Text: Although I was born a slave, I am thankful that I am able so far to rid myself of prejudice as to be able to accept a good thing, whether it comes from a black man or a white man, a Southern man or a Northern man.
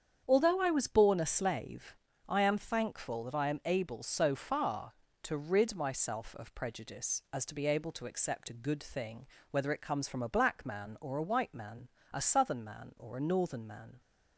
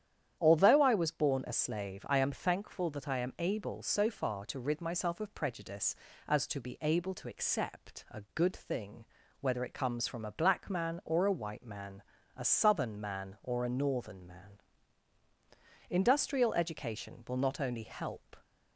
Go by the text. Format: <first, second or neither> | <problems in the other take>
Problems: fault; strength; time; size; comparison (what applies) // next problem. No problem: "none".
first | starts louder than the rest; strong; until 1.4 s; 10 dB; strong in the first // goes on to say "Industrial education will not only help"; strong; from 15.8 s on; 2.4 s long